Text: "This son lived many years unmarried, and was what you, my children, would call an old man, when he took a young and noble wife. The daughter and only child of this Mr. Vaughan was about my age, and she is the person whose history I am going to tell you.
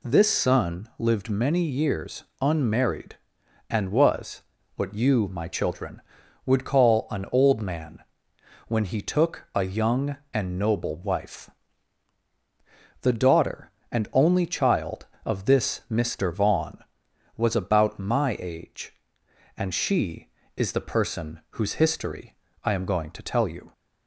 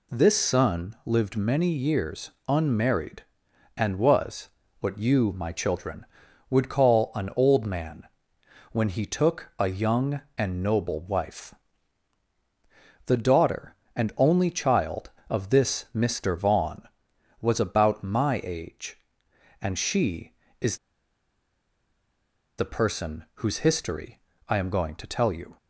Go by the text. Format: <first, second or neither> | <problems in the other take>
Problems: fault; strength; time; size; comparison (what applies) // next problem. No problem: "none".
first | pauses between "years" and "unmarried"; slight; at 2.3 s; 0.16 s long; slight in the first // pauses between "was" and "what"; slight; at 4.4 s; 0.32 s long; slight in the first // pauses between "is" and "the"; strong; at 20.7 s; 1.8 s long // pauses between "history" and "I"; slight; at 24.1 s; 0.28 s long; slight in the first